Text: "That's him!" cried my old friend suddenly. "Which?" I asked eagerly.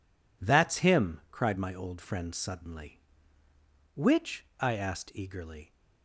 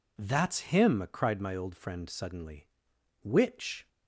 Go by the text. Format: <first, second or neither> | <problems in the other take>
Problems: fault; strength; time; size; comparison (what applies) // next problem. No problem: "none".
first | stops before "I asked eagerly"; at 3.8 s